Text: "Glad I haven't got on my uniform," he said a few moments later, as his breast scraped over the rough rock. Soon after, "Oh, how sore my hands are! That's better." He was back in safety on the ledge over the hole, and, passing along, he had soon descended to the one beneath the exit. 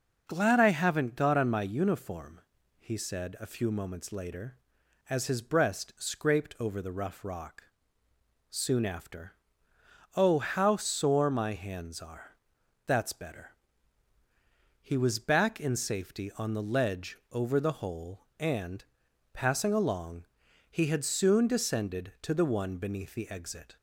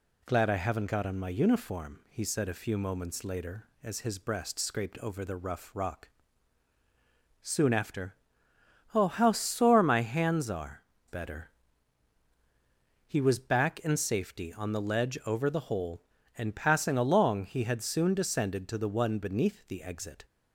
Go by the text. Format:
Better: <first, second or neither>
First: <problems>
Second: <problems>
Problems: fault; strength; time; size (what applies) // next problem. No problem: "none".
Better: first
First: none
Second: skips "That's"; at 10.9 s